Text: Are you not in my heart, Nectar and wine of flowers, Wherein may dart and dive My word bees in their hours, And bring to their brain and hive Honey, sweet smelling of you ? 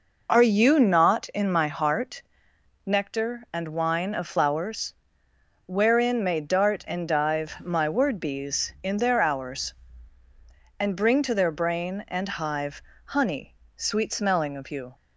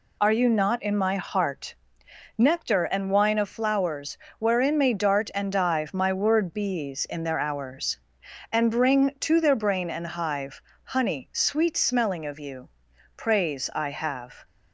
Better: first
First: pauses between "hive" and "Honey"; slight; at 12.8 s; 0.26 s long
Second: pauses between "hive" and "Honey"; slight; at 10.6 s; 0.22 s long // goes on to say "Praise I have"; noticeable; from 13.1 s on; 1.3 s long

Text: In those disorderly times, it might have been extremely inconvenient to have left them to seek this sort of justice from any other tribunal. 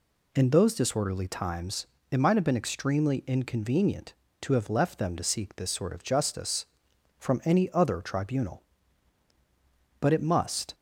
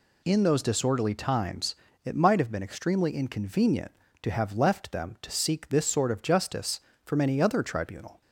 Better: second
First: goes on to say "But it must"; noticeable; from 9.9 s on; 0.76 s long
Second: none

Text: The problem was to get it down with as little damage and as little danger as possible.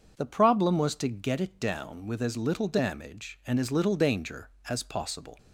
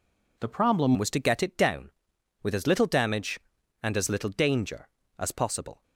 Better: first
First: none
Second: changes voice at "was"; from 0.9 s on; 4.9 s long

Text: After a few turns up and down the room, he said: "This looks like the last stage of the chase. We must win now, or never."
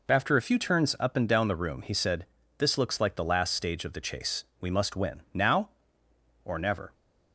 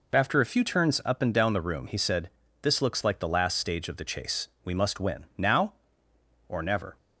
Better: neither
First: none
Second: none

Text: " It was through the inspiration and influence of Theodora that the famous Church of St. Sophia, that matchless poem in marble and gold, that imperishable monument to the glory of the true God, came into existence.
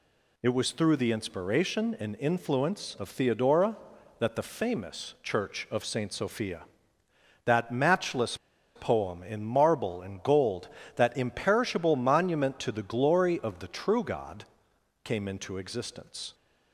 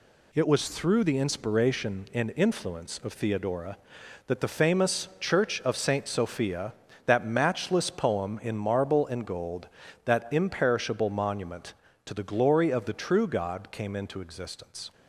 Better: second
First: pauses between "matchless" and "poem"; at 8.3 s; 0.38 s long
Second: none

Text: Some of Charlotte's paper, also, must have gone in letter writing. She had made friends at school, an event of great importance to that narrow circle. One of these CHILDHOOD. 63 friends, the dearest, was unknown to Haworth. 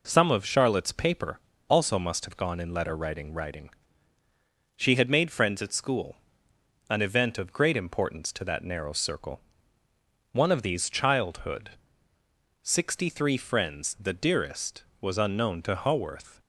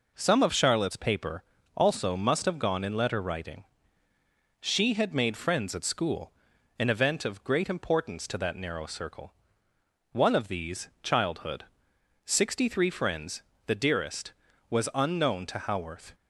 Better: second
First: says "writing" twice; at 3.3 s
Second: none

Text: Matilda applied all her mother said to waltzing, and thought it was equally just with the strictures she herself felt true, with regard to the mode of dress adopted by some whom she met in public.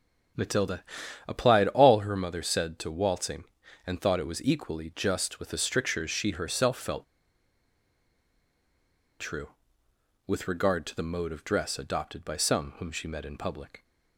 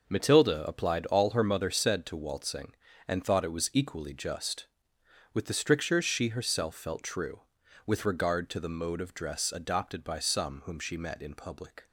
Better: second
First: starts louder than the rest; noticeable; until 1.8 s; 6 dB // pauses between "Matilda" and "applied"; at 0.8 s; 0.44 s long // pauses between "felt" and "true"; strong; at 7.0 s; 2.1 s long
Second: none

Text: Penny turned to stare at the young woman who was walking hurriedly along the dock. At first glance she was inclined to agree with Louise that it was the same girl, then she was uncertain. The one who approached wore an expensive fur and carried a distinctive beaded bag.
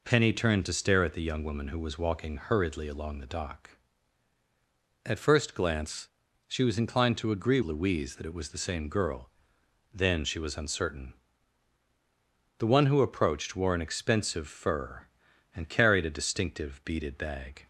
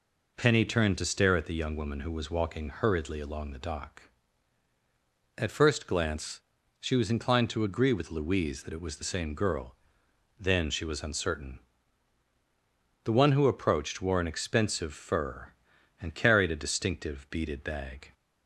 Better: second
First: pauses between "glance" and "she"; at 6.0 s; 0.40 s long // skips "with"; at 7.6 s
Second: pauses between "glance" and "she"; at 6.4 s; 0.40 s long

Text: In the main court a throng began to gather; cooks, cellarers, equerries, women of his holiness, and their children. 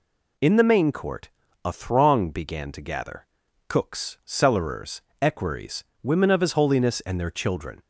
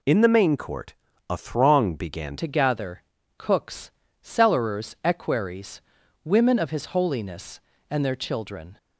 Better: first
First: pauses between "court" and "a"; slight; at 1.2 s; 0.36 s long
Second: pauses between "court" and "a"; slight; at 0.9 s; 0.36 s long // changes voice at "to"; from 2.3 s on; 6.4 s long

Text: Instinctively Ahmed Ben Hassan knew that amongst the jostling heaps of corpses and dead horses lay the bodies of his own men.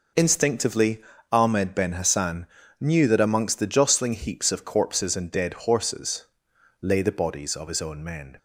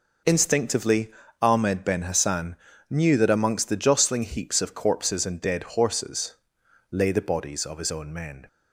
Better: neither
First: pauses between "Instinctively" and "Ahmed"; slight; at 1.0 s; 0.30 s long // pauses between "Hassan" and "knew"; slight; at 2.4 s; 0.34 s long // pauses between "horses" and "lay"; noticeable; at 6.2 s; 0.56 s long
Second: pauses between "Instinctively" and "Ahmed"; slight; at 1.1 s; 0.30 s long // pauses between "Hassan" and "knew"; slight; at 2.5 s; 0.34 s long // pauses between "horses" and "lay"; noticeable; at 6.3 s; 0.56 s long

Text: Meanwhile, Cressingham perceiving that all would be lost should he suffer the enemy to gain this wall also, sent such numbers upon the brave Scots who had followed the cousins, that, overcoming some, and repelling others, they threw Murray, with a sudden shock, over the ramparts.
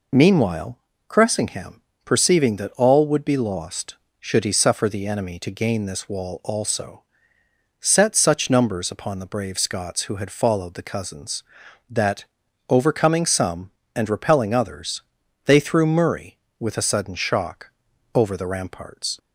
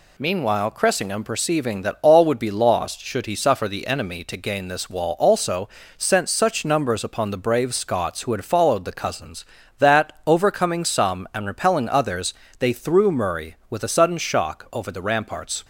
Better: second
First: pauses between "Cressingham" and "perceiving"; slight; at 1.8 s; 0.22 s long // says "set" for "sent"; at 7.7 s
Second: none

